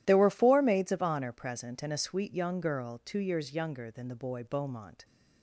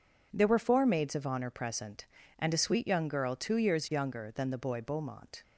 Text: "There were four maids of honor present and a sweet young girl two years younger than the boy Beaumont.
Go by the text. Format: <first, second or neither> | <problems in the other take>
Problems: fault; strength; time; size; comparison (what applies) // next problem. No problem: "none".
neither | none